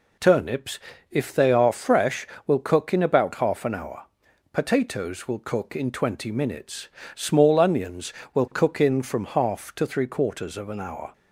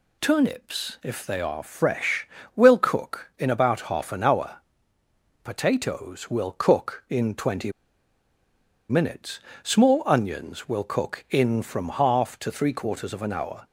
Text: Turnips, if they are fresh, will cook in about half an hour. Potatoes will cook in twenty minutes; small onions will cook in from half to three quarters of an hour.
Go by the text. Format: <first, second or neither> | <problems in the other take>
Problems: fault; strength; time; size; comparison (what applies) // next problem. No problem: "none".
first | pauses between "twenty" and "minutes"; at 7.7 s; 1.1 s long